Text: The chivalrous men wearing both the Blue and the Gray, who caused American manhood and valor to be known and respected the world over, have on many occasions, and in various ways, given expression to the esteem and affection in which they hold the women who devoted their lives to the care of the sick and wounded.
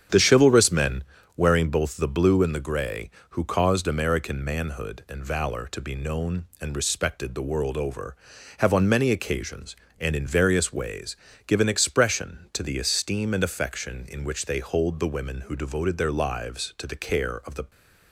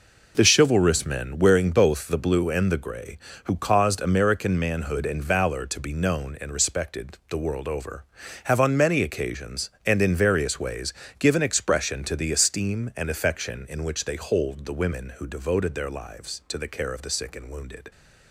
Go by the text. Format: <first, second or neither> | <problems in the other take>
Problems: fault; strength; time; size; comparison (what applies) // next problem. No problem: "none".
second | starts louder than the rest; strong; until 1.4 s; 8 dB // pauses between "men" and "wearing"; slight; at 1.0 s; 0.32 s long // stops before "sick and wounded"; at 17.6 s